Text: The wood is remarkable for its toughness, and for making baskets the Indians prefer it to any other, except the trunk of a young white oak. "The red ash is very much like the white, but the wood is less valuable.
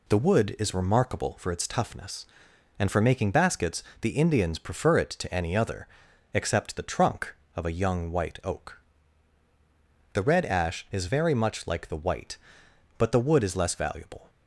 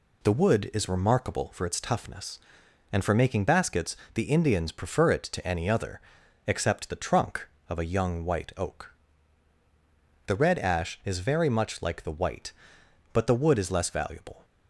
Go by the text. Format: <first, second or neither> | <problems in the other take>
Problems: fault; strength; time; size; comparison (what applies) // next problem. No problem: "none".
neither | pauses between "baskets" and "the"; slight; the same in both